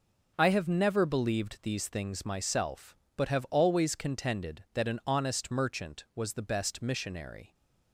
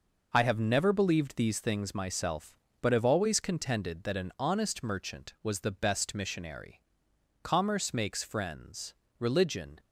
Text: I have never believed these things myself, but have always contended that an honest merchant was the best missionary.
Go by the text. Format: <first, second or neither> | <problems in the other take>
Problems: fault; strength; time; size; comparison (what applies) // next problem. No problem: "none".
first | goes on to say "Commerce makes friends religion"; strong; from 7.4 s on; 2.3 s long